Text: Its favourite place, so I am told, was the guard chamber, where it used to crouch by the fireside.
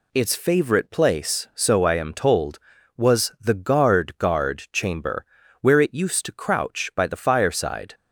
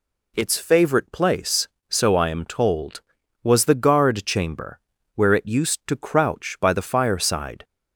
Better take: second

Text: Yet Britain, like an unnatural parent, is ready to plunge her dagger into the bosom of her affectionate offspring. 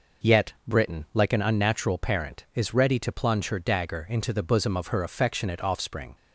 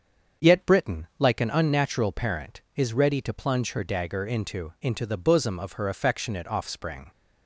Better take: first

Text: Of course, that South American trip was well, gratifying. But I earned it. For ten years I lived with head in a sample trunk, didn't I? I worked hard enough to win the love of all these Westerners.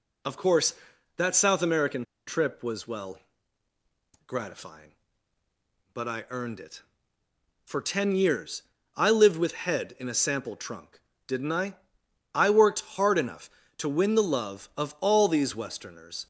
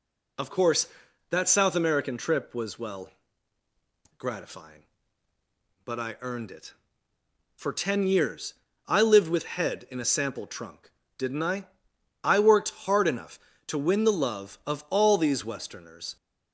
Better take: second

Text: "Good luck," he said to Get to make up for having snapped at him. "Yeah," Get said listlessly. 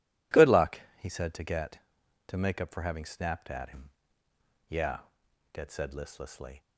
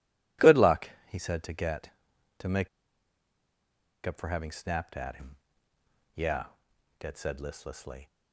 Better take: first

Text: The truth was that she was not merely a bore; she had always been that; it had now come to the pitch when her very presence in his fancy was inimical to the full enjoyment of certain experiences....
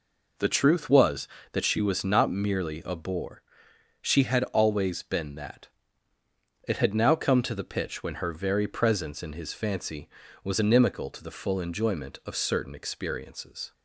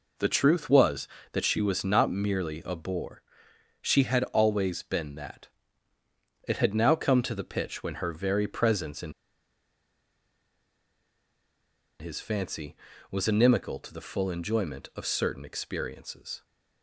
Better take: first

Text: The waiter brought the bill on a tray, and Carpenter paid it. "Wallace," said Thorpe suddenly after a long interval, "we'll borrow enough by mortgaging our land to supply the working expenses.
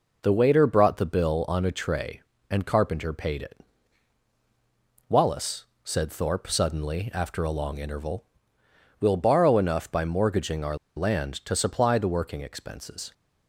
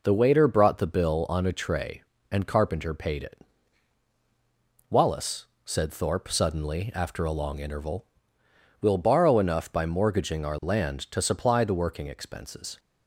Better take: second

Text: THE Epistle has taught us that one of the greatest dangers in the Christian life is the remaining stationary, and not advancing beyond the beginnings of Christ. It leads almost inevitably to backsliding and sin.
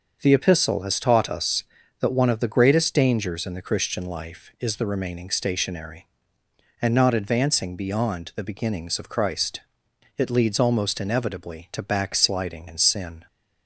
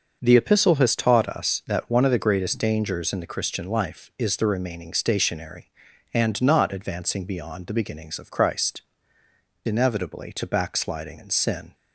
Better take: first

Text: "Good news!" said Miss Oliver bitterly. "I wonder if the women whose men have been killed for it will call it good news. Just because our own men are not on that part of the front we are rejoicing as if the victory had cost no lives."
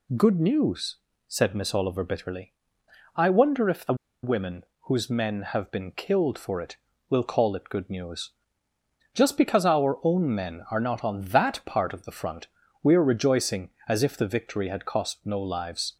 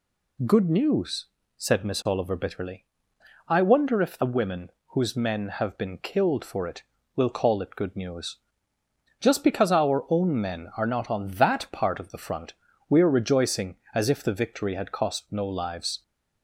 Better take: second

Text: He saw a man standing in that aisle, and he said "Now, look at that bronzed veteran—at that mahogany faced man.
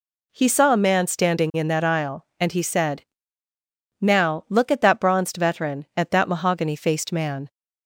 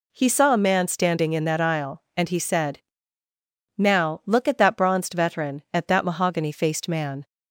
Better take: neither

